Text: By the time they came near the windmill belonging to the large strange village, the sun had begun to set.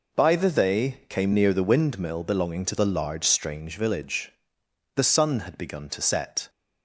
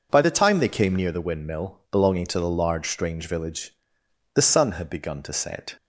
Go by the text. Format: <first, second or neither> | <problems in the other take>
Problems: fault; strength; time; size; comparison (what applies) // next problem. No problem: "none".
second | skips "time"; at 0.5 s